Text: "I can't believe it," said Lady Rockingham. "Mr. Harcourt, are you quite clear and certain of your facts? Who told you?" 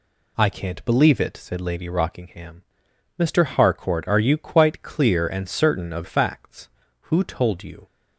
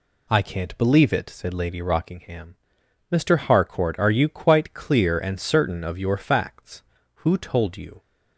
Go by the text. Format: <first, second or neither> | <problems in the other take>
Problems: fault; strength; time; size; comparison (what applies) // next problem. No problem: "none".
second | skips "your"; at 6.0 s